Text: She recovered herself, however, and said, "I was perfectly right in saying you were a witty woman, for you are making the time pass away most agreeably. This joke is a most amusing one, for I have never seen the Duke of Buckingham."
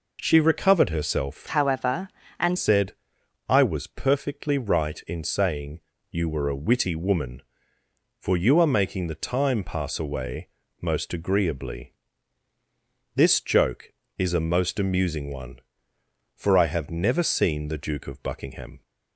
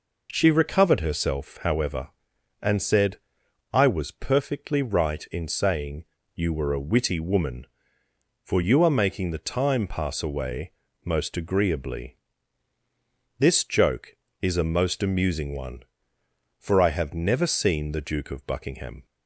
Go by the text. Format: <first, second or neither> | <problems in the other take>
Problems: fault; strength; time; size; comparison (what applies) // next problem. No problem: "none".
second | changes voice from "however" to "and"; from 1.4 to 2.5 s; 1.1 s long // pauses between "saying" and "you"; slight; at 5.7 s; 0.32 s long; slight in the second // pauses between "away" and "most"; slight; at 10.4 s; 0.32 s long; slight in the second